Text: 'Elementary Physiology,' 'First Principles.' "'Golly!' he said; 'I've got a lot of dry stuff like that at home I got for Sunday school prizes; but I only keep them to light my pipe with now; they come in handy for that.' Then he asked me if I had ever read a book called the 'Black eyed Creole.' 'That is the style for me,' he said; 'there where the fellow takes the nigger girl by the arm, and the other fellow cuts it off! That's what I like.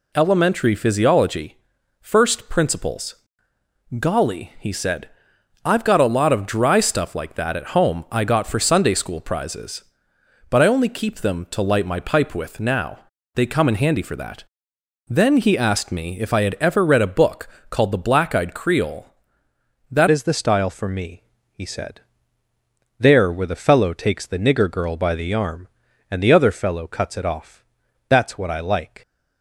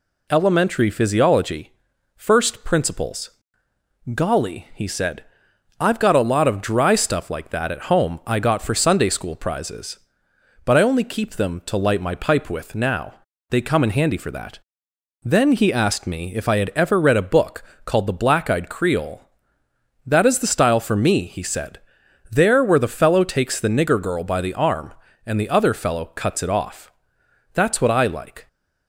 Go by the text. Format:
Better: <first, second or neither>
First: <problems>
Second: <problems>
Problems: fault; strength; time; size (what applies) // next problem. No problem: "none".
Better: second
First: pauses between "book" and "called"; slight; at 17.4 s; 0.22 s long // changes voice at "is"; from 20.0 s on; 9.0 s long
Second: pauses between "book" and "called"; slight; at 17.6 s; 0.22 s long